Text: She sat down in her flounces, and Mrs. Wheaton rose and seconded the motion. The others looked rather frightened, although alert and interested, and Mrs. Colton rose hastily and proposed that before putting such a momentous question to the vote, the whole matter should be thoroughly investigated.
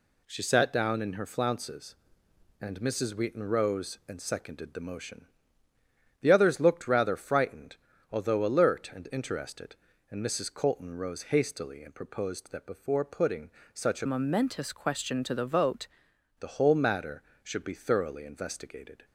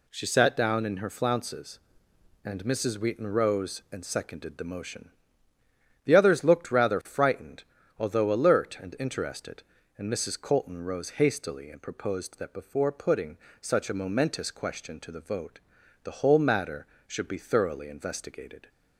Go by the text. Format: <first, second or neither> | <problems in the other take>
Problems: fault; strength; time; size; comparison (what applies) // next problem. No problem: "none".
second | pauses between "putting" and "such"; slight; at 13.4 s; 0.24 s long; slight in the second // changes voice from "momentous" to "vote"; from 14.0 to 15.8 s; 1.8 s long